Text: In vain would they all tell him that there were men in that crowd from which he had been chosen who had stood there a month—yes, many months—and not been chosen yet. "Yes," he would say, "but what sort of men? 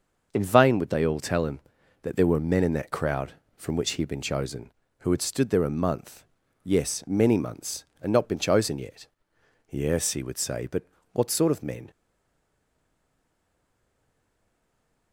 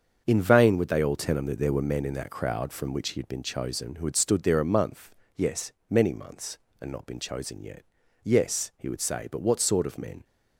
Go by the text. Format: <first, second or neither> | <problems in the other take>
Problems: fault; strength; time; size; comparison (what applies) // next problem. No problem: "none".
second | starts louder than the rest; noticeable; until 1.3 s; 6 dB; also in the second // pauses between "but" and "what"; slight; at 10.8 s; 0.28 s long // stays silent after the last word; strong; from 11.9 s on; 3.2 s long